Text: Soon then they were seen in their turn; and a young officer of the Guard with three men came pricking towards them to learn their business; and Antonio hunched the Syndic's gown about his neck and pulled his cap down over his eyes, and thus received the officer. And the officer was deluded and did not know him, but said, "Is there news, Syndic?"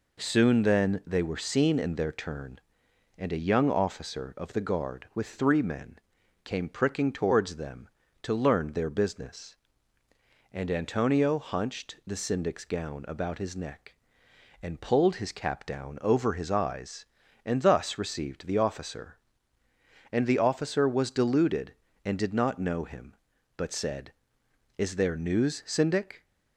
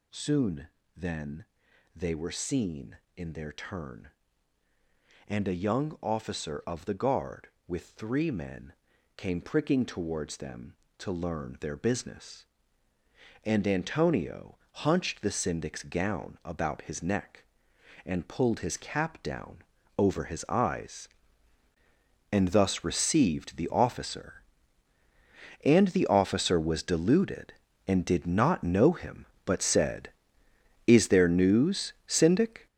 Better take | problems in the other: first | gets louder; strong; throughout; 8.5 dB // pauses between "Soon" and "then"; slight; at 0.6 s; 0.30 s long // pauses between "then" and "they"; noticeable; at 1.4 s; 0.50 s long // pauses between "men" and "came"; at 8.7 s; 0.44 s long; also in the first // pauses between "Antonio" and "hunched"; slight; at 14.5 s; 0.16 s long // pauses between "down" and "over"; at 19.5 s; 0.38 s long

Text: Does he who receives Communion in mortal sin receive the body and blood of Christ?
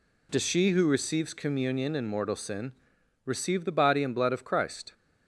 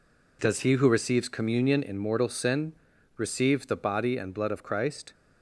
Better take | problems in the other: second | says "she" for "he"; at 0.4 s // pauses between "sin" and "receive"; noticeable; at 2.7 s; 0.54 s long; noticeable in the second

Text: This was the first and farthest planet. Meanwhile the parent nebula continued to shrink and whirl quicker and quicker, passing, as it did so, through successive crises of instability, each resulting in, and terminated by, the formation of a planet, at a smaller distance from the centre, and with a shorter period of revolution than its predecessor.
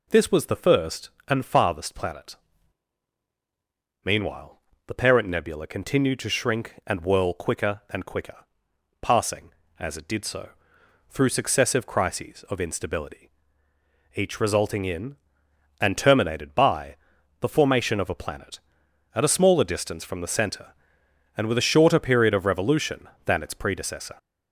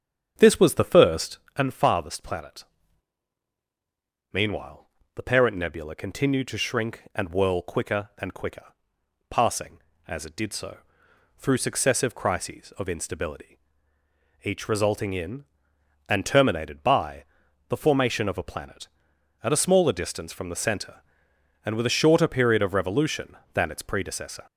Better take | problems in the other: first | starts louder than the rest; strong; until 1.6 s; 8 dB // pauses between "Meanwhile" and "the"; slight; at 4.8 s; 0.32 s long; slight in the first

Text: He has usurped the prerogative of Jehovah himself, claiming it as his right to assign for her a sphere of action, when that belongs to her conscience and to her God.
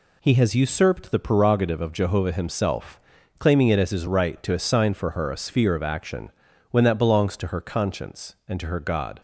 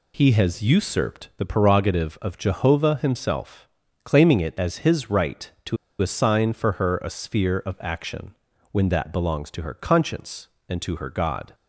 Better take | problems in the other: first | pauses between "to" and "assign"; slight; at 5.7 s; 0.23 s long

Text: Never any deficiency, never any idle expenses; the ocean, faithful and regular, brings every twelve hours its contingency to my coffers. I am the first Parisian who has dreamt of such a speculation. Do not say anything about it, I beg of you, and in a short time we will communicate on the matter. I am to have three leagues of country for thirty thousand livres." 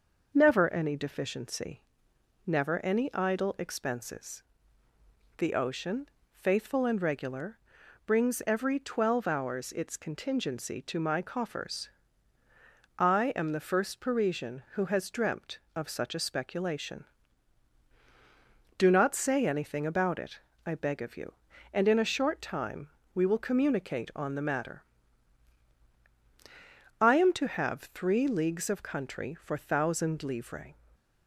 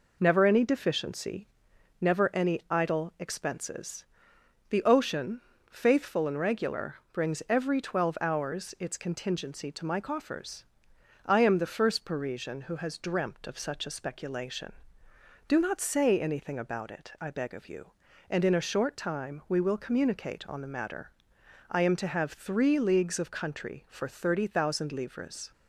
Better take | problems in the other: second | pauses between "time" and "we"; slight; at 22.8 s; 0.24 s long // skips "thirty"; at 29.5 s

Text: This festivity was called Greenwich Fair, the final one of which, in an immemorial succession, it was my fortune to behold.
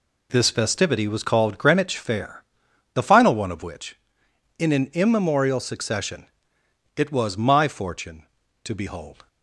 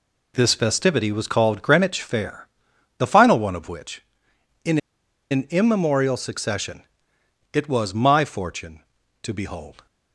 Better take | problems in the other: first | pauses between "in" and "an"; noticeable; at 4.7 s; 0.53 s long

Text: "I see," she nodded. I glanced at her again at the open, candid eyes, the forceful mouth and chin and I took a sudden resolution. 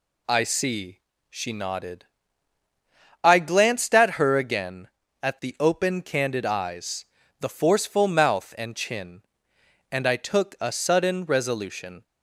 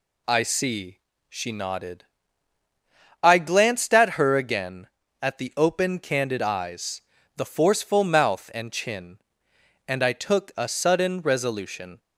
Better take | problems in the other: neither | none

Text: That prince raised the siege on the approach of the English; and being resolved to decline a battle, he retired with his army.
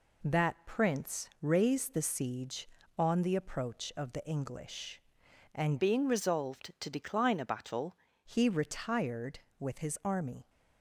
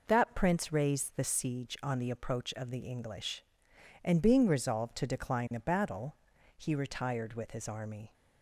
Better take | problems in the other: second | changes voice from "being" to "battle"; from 5.8 to 7.9 s; 2.1 s long

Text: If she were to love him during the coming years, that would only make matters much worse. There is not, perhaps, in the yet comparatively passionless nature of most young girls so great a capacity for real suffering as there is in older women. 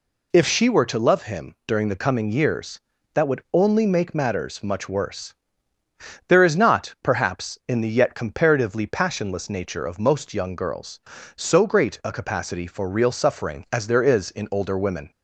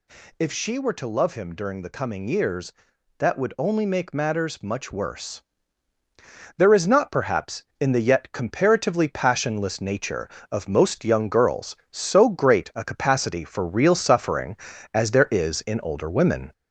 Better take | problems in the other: first | gets louder; slight; throughout; 3 dB

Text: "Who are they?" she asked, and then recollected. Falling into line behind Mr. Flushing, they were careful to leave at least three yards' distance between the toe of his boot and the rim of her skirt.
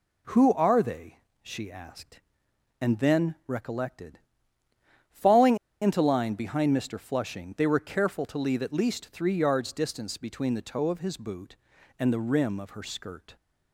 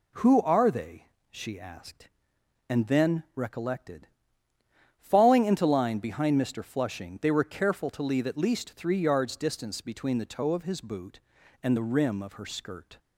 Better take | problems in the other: second | pauses between "Falling" and "into"; slight; at 5.5 s; 0.25 s long

